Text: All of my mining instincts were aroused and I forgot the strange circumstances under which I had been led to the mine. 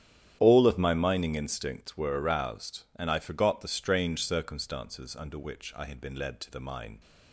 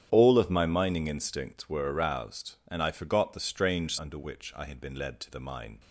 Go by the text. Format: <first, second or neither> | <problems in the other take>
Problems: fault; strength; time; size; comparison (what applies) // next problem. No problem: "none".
first | starts louder than the rest; strong; until 1.1 s; 10 dB; strong in the first // skips "circumstances"; at 3.9 s